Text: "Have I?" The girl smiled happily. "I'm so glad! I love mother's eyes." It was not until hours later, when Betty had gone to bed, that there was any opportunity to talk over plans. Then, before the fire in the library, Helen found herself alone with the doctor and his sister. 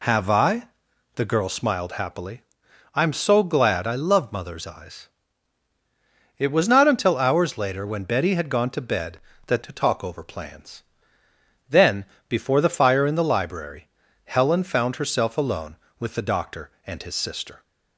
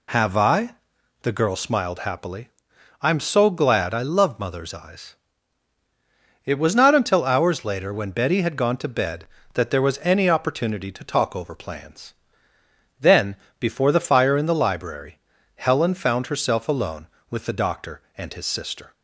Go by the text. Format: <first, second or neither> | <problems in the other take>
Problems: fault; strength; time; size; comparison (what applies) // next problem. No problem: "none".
second | skips "there was any opportunity"; at 9.6 s